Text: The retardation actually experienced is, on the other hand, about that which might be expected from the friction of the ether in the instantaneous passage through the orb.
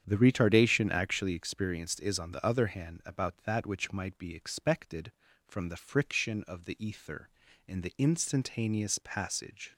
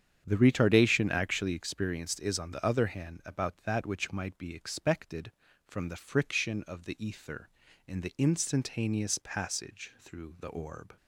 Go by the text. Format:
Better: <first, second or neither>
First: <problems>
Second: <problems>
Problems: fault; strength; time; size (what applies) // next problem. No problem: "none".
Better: second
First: starts louder than the rest; strong; until 1.0 s; 8 dB // stops before "through the orb"; at 9.7 s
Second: starts louder than the rest; strong; until 1.2 s; 8.5 dB